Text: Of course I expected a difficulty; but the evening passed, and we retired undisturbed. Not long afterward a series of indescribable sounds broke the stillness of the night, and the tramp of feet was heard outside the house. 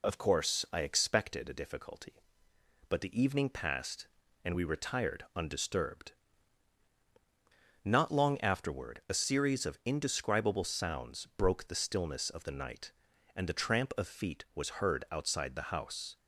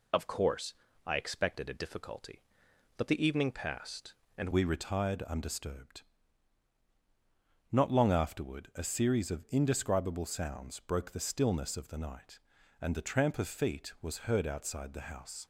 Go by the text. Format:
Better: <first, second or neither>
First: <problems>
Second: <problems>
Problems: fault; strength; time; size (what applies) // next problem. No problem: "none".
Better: first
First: none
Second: pauses between "course" and "I"; slight; at 0.7 s; 0.32 s long // changes voice at "we"; from 4.5 s on; 10.9 s long